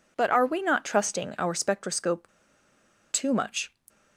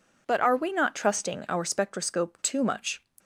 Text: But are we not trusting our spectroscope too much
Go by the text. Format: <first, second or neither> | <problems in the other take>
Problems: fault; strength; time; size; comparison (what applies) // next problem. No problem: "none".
second | pauses between "spectroscope" and "too"; noticeable; at 2.2 s; 0.83 s long